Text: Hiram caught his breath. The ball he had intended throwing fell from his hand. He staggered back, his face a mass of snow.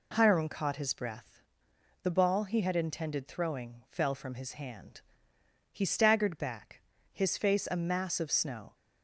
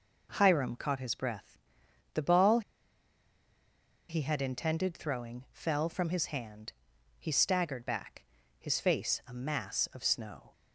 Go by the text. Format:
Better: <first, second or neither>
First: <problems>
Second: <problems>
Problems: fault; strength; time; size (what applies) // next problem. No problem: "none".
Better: first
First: none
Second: pauses between "ball" and "he"; strong; at 2.6 s; 1.4 s long